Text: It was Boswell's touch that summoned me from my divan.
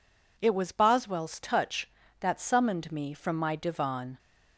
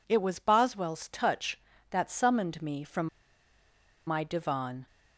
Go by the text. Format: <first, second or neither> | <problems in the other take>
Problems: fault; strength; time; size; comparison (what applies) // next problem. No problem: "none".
first | pauses between "from" and "my"; at 3.0 s; 1.0 s long